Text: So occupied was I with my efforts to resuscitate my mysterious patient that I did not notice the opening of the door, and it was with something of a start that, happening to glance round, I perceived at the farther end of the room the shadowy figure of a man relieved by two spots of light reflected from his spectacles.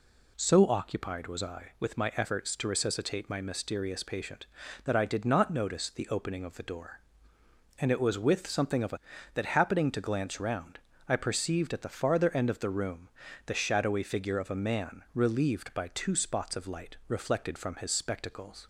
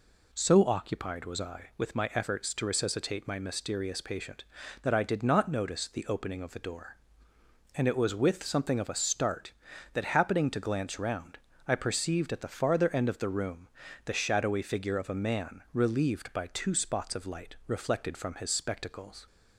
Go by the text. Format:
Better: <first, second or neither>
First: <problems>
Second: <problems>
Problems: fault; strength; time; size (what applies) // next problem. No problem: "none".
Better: second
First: skips "start"; at 9.1 s // pauses between "room" and "the"; slight; at 13.0 s; 0.36 s long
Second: pauses between "room" and "the"; slight; at 13.6 s; 0.36 s long